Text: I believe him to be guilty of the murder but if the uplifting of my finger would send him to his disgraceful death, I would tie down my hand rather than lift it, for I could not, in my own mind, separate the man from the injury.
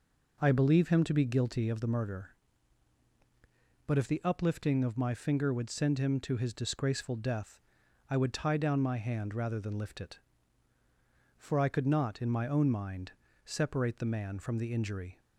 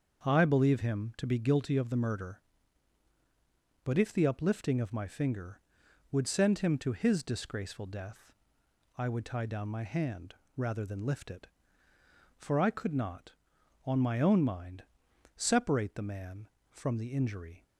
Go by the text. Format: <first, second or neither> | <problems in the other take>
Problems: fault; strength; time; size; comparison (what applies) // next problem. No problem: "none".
first | starts louder than the rest; until 1.2 s; 6.5 dB // pauses between "hand" and "rather"; slight; at 10.3 s; 0.20 s long // says "on" for "in"; at 13.8 s